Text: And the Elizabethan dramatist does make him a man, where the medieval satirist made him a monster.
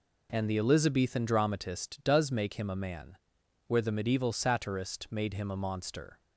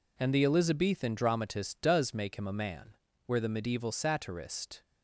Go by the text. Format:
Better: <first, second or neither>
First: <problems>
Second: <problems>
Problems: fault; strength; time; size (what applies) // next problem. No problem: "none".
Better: first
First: none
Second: stops before "made him a monster"; at 4.8 s